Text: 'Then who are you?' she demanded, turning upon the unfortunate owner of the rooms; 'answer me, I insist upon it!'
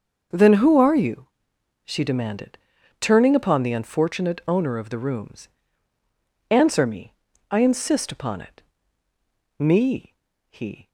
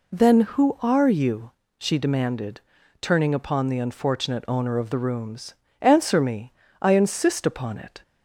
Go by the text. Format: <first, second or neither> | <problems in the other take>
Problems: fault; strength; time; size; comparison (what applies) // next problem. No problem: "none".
second | starts louder than the rest; until 1.8 s; 6 dB // goes on to say "Me he"; noticeable; from 9.5 s on; 1.2 s long